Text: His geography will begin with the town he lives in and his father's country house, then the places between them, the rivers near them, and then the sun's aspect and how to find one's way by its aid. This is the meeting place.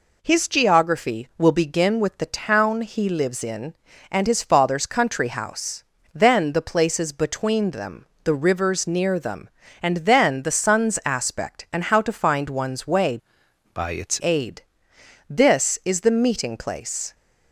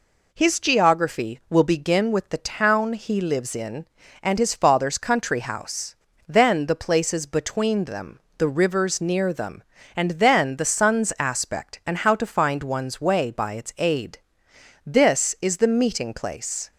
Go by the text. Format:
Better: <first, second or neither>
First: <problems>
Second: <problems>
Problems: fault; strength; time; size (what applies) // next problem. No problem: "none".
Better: second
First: changes voice from "by" to "its"; from 13.7 to 14.2 s; 0.5 s long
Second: none